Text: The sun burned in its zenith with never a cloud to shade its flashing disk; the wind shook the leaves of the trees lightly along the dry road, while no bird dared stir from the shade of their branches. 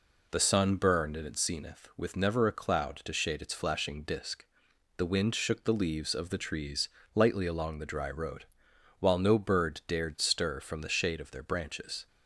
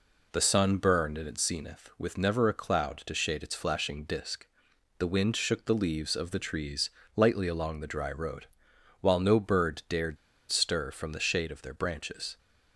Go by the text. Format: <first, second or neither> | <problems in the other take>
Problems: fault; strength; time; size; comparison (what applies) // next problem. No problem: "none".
first | pauses between "trees" and "lightly"; slight; at 6.9 s; 0.24 s long; slight in the first // pauses between "dared" and "stir"; slight; at 10.1 s; 0.34 s long